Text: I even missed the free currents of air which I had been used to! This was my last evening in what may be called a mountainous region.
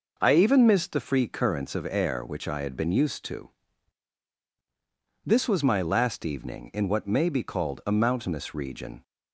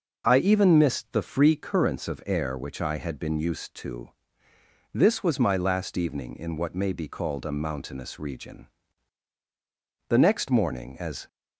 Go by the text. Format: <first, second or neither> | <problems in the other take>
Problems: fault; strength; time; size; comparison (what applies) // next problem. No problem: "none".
first | goes on to say "The next morning as"; noticeable; from 10.0 s on; 1.2 s long